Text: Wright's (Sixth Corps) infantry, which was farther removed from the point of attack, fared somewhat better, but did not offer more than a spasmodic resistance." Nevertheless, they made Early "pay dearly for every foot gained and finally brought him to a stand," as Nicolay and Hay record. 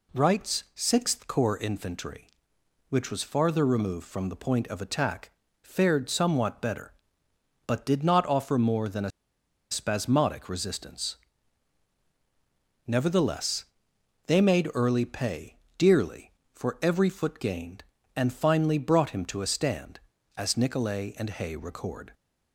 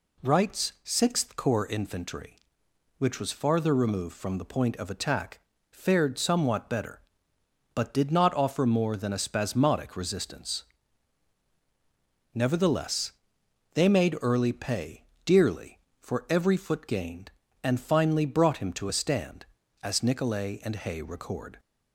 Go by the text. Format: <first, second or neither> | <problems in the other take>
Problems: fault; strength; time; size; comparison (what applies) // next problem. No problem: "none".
second | pauses between "a" and "spasmodic"; noticeable; at 9.1 s; 0.60 s long // pauses between "pay" and "dearly"; slight; at 15.5 s; 0.22 s long; slight in the second